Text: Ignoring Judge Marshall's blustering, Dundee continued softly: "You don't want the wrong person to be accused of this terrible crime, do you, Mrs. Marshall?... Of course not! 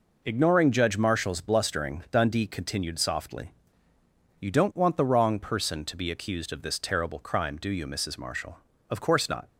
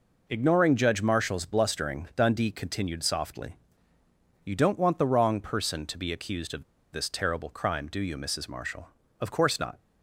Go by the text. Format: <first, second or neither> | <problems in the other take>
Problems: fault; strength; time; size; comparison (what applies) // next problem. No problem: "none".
first | pauses between "of" and "this"; slight; at 6.6 s; 0.29 s long